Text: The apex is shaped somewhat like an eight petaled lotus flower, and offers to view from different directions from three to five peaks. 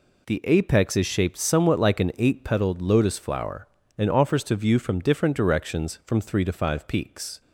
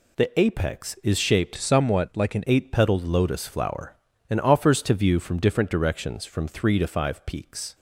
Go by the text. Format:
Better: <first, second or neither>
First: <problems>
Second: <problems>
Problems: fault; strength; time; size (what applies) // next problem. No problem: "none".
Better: first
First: none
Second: changes voice from "somewhat" to "an"; from 1.5 to 2.4 s; 0.9 s long